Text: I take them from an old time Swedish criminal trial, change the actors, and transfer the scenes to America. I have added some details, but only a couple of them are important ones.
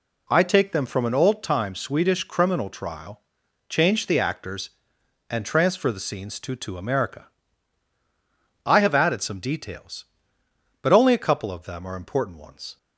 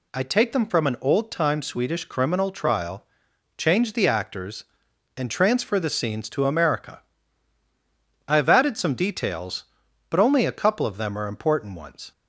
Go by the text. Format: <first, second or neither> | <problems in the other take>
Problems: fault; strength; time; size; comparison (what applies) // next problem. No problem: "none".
second | says "to" twice; at 6.5 s